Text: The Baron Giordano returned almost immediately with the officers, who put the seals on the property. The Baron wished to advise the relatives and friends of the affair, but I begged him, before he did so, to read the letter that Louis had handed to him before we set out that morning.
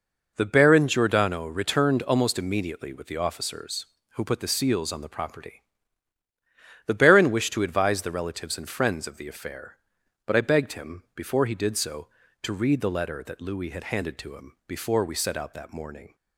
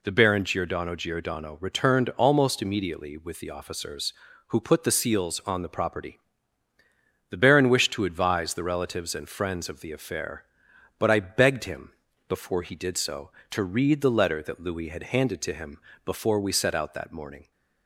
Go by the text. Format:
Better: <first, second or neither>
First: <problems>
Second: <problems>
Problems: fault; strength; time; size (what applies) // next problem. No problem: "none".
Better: first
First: none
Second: says "Giordano" twice; at 0.9 s // pauses between "him" and "before"; slight; at 15.7 s; 0.30 s long